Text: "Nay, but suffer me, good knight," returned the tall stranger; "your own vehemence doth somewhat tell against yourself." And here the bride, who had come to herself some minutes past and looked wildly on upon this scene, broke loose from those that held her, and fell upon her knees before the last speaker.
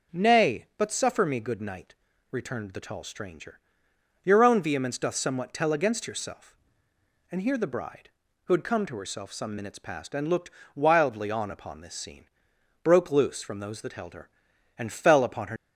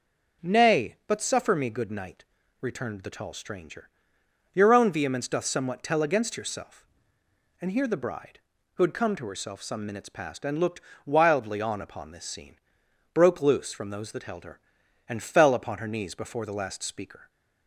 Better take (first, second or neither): second